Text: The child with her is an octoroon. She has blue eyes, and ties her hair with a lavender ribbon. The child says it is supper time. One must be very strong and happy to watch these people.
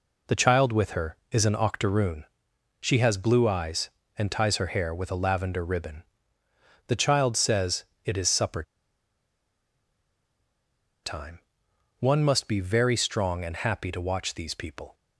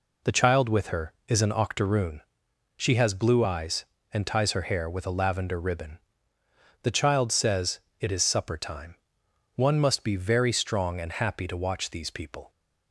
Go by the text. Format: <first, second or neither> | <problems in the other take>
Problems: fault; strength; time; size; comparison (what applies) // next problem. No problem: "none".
second | pauses between "says" and "it"; slight; at 7.8 s; 0.22 s long; slight in the second // pauses between "supper" and "time"; strong; at 8.6 s; 2.4 s long